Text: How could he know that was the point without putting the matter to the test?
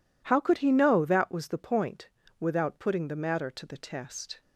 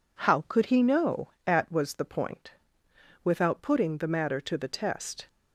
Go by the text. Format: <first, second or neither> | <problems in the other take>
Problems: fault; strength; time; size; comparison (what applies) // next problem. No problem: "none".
first | says "at" for "that"; at 1.4 s // pauses between "point" and "without"; noticeable; at 2.4 s; 0.74 s long; slight in the first